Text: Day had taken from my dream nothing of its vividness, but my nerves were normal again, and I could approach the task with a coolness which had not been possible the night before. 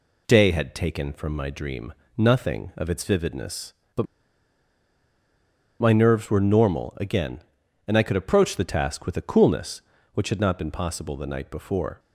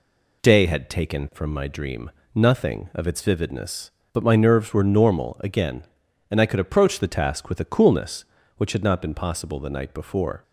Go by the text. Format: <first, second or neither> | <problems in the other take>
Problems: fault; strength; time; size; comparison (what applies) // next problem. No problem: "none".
second | pauses between "dream" and "nothing"; slight; at 1.9 s; 0.24 s long; slight in the second // pauses between "but" and "my"; strong; at 4.0 s; 1.7 s long